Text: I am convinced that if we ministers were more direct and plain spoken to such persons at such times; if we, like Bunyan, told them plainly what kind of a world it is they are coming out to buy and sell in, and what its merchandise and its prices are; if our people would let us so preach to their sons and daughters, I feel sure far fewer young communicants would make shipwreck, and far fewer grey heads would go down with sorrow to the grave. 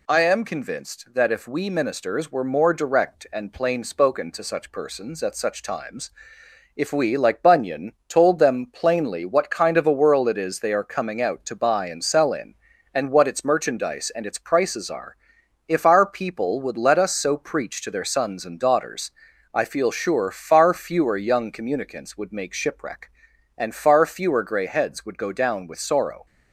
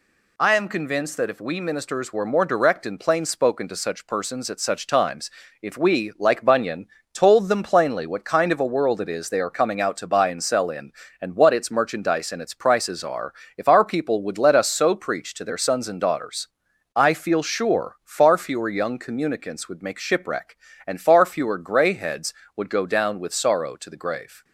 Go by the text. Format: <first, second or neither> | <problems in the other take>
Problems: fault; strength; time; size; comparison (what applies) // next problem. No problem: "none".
second | stops before "to the grave"; at 26.2 s